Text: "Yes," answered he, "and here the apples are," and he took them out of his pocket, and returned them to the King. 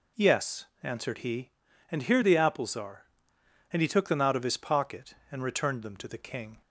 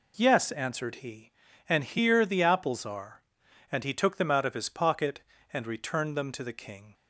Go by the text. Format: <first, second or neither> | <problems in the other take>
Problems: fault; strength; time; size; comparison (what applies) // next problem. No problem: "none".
neither | none